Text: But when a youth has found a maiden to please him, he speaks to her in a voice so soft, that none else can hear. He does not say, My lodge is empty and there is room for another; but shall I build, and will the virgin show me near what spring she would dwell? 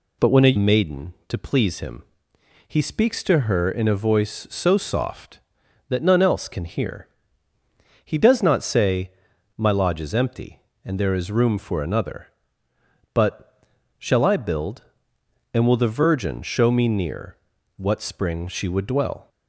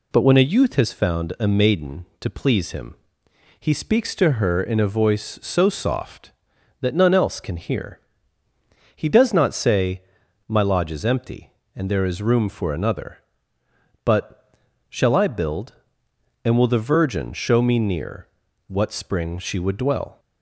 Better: second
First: skips "youth has found a"; at 0.5 s // pauses between "but" and "shall"; slight; at 13.6 s; 0.34 s long // pauses between "near" and "what"; at 17.3 s; 0.40 s long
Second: pauses between "but" and "shall"; slight; at 14.5 s; 0.34 s long // pauses between "near" and "what"; at 18.2 s; 0.40 s long

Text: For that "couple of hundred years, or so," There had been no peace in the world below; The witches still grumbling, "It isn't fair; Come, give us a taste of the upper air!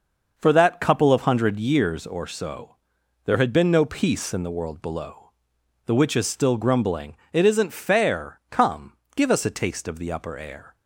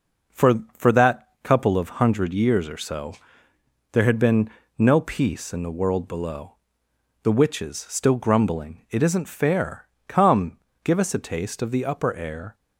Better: first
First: none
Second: says "For" twice; at 0.7 s // pauses between "been" and "no"; slight; at 4.4 s; 0.30 s long

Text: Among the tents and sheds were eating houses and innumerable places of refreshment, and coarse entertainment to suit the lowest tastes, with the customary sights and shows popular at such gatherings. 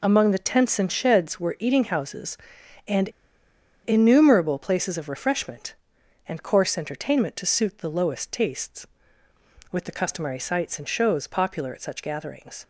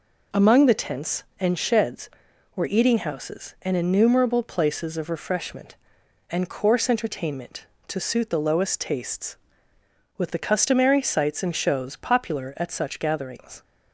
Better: second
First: pauses between "and" and "innumerable"; noticeable; at 3.0 s; 0.75 s long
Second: none

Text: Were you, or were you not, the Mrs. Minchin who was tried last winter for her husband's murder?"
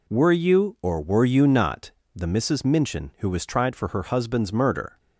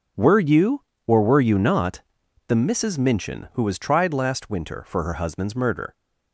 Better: second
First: skips "last winter"; at 3.7 s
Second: none

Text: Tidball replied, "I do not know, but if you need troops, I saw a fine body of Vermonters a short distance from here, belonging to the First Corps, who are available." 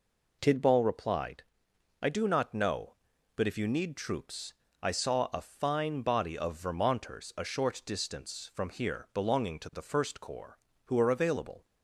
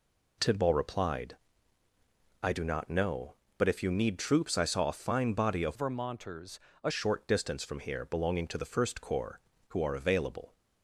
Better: first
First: none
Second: changes voice from "Vermonters" to "a"; from 5.7 to 6.9 s; 1.2 s long // pauses between "Vermonters" and "a"; slight; at 6.6 s; 0.24 s long

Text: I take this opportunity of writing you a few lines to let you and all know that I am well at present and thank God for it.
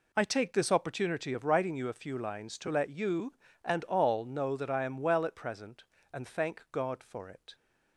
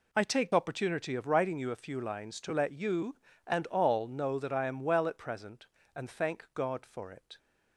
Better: first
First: none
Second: skips "this"; at 0.5 s

